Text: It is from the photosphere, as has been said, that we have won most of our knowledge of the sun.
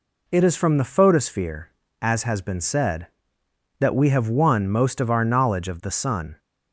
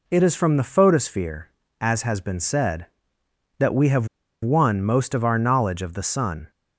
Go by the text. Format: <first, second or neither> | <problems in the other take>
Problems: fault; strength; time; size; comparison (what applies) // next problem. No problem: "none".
first | pauses between "have" and "won"; at 4.0 s; 0.36 s long